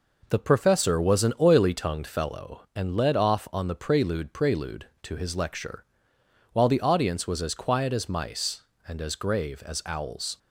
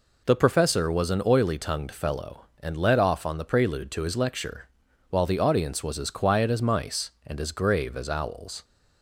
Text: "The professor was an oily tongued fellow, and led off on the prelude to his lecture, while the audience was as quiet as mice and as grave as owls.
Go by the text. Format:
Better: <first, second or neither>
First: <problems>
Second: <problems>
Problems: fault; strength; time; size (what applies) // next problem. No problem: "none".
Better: second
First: says "prelude" twice; at 4.3 s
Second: none